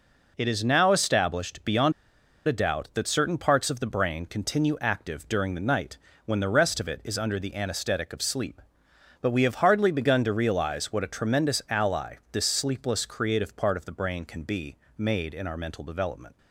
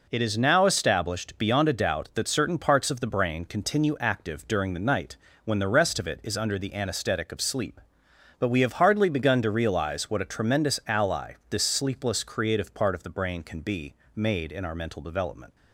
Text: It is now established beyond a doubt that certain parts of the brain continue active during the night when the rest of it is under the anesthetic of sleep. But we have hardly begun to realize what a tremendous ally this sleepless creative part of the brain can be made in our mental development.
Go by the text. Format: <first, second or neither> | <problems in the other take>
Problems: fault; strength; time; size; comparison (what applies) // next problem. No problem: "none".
second | pauses between "beyond" and "a"; noticeable; at 1.9 s; 0.54 s long // pauses between "night" and "when"; slight; at 5.9 s; 0.28 s long; slight in the second // pauses between "ally" and "this"; slight; at 12.1 s; 0.16 s long; slight in the second // pauses between "be" and "made"; slight; at 14.7 s; 0.20 s long; slight in the second